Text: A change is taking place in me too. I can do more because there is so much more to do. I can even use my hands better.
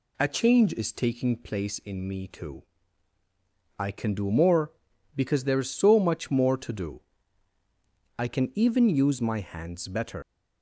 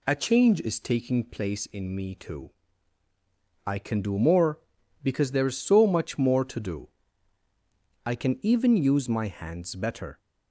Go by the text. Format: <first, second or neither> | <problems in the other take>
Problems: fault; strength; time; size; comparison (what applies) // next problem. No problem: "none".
second | leaves "better" unfinished; at 10.2 s; 85 ms